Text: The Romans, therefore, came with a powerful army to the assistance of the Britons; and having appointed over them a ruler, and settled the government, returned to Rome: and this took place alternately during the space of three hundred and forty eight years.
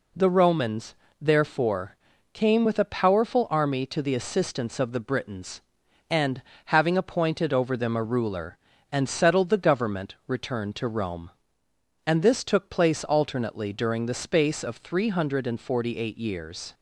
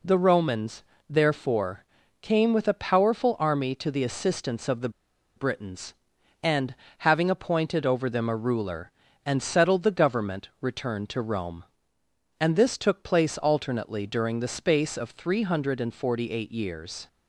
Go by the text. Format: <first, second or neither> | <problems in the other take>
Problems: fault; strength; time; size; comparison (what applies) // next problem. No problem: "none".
first | pauses between "the" and "Britons"; noticeable; at 4.8 s; 0.46 s long // pauses between "and" and "having"; slight; at 6.7 s; 0.24 s long; slight in the first